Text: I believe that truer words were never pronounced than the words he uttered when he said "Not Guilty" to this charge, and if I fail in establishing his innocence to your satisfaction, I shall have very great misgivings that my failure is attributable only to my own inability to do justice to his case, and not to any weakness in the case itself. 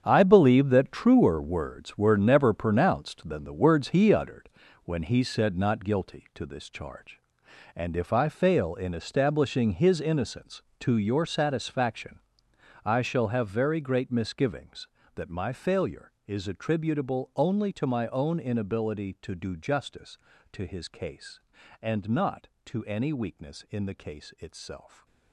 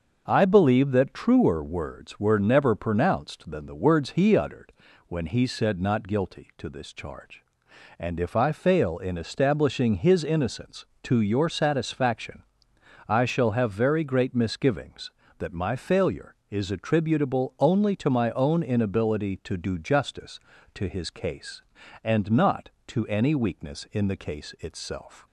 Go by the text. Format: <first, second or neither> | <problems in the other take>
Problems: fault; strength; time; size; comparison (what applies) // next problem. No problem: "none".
second | gets quieter; strong; throughout; 11.5 dB // starts louder than the rest; strong; until 1.0 s; 8 dB; also in the second // pauses between "uttered" and "when"; slight; at 4.4 s; 0.34 s long; slight in the second // stays silent after the last word; slight; from 24.8 s on; 0.5 s long